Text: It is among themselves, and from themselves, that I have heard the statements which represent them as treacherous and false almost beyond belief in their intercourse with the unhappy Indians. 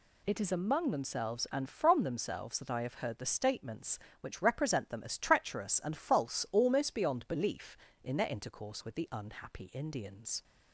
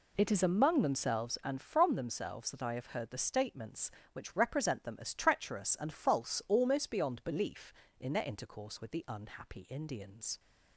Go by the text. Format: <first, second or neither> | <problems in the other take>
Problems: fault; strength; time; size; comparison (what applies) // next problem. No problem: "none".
first | starts louder than the rest; slight; until 1.3 s; 3 dB